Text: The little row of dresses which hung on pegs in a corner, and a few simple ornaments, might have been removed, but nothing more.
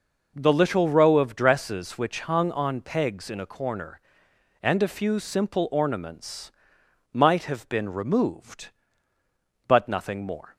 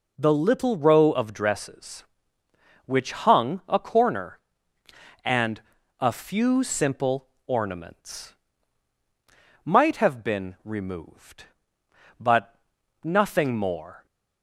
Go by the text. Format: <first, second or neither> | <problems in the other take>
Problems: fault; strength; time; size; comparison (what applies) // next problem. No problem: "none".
first | skips "on pegs in"; at 3.6 s // pauses between "and" and "a"; at 5.5 s; 0.38 s long // pauses between "simple" and "ornaments"; slight; at 7.2 s; 0.20 s long // pauses between "but" and "nothing"; noticeable; at 12.5 s; 0.48 s long